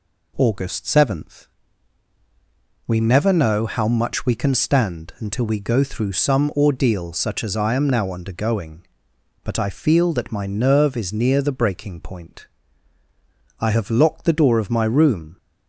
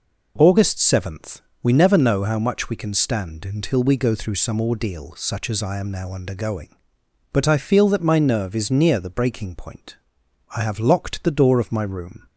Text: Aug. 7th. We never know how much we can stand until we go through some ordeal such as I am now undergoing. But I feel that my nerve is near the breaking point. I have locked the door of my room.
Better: neither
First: none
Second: none

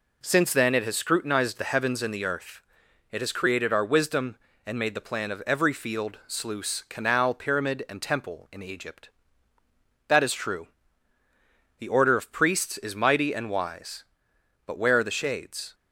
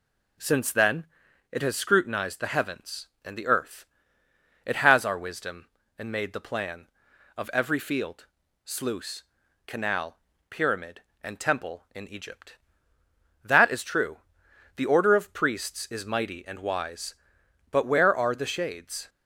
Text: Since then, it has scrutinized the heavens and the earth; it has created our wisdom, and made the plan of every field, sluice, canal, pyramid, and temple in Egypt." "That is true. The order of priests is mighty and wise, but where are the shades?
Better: first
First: none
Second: skips "created"; at 5.0 s

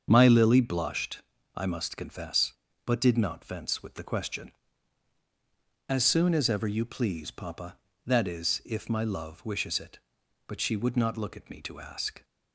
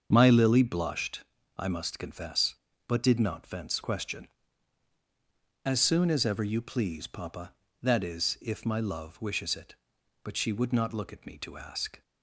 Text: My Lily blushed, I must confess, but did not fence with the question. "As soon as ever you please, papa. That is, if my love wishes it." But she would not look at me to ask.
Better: first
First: starts louder than the rest; until 1.1 s; 7 dB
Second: starts louder than the rest; until 1.1 s; 6.5 dB // skips "with the"; at 3.8 s

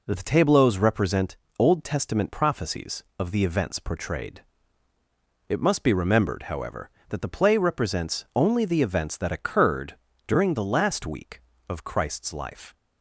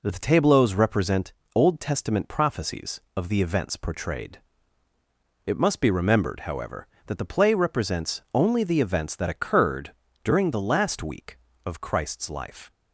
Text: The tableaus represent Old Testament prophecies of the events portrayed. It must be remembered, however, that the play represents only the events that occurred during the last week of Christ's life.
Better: neither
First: pauses between "represent" and "Old"; slight; at 1.3 s; 0.20 s long // pauses between "occurred" and "during"; slight; at 9.9 s; 0.32 s long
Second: pauses between "represent" and "Old"; slight; at 1.3 s; 0.20 s long // pauses between "occurred" and "during"; slight; at 9.8 s; 0.32 s long

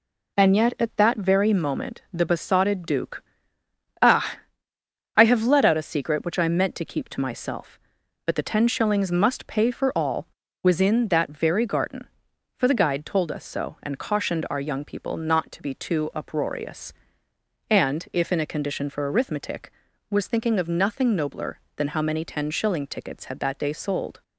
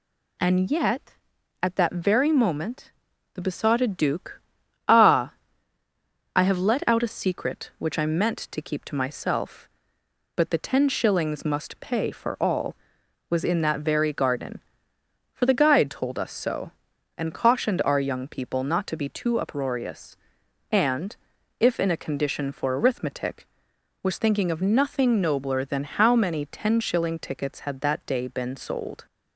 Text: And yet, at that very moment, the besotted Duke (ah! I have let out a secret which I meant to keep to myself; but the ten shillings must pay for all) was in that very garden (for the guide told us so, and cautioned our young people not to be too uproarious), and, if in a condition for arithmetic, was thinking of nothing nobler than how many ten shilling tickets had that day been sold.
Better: second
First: skips "been"; at 23.7 s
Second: none

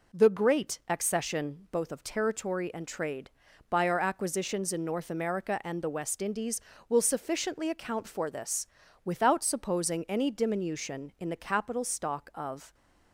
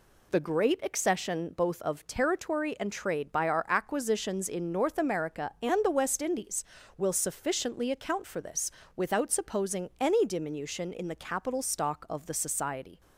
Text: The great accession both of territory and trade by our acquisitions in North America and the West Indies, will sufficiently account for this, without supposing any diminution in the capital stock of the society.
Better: second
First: stops before "the society"; at 12.7 s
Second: none

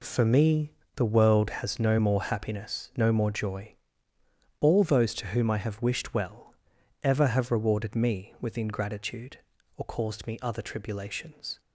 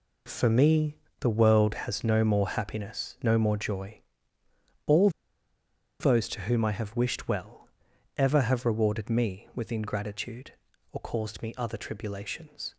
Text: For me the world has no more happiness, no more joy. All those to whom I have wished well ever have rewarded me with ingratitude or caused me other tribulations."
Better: first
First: pauses between "me" and "the"; slight; at 0.7 s; 0.22 s long // pauses between "well" and "ever"; noticeable; at 6.5 s; 0.48 s long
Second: pauses between "me" and "the"; slight; at 0.9 s; 0.22 s long // pauses between "All" and "those"; noticeable; at 5.0 s; 0.91 s long // pauses between "well" and "ever"; noticeable; at 7.6 s; 0.48 s long

